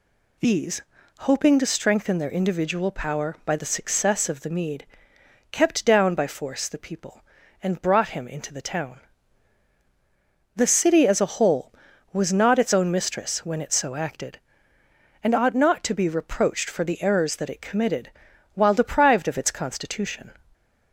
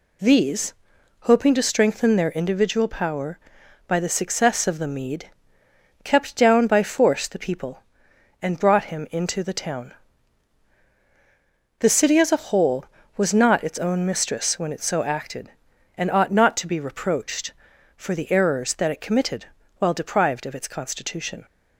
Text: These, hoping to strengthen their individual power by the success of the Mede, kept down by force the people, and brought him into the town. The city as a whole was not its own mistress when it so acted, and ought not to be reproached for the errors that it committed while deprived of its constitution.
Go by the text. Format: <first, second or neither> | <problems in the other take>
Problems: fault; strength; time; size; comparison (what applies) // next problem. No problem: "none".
neither | pauses between "committed" and "while"; the same in both